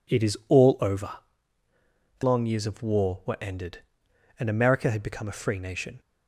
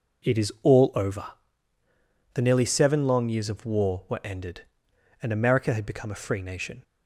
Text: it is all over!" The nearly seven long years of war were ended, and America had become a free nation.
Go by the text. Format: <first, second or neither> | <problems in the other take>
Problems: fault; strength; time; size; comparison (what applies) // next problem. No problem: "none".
second | skips "nearly seven"; at 2.2 s